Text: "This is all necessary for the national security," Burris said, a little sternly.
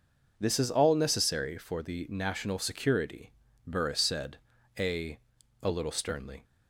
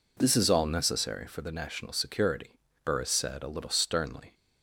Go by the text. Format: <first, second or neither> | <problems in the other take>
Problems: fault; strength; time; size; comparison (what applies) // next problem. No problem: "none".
second | says "a" twice; at 5.6 s